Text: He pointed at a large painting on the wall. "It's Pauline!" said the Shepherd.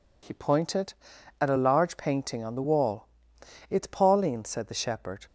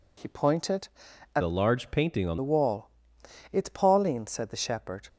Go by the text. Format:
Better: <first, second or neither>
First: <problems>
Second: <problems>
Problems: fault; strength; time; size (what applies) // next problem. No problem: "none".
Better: first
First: none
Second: changes voice from "a" to "on"; from 1.4 to 2.3 s; 0.9 s long